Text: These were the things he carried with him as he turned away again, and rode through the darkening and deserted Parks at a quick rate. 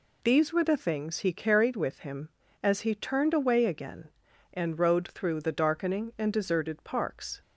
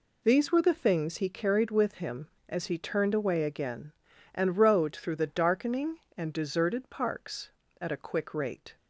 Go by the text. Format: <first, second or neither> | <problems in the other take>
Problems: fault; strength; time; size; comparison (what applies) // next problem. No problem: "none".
second | stops before "at a quick rate"; at 7.4 s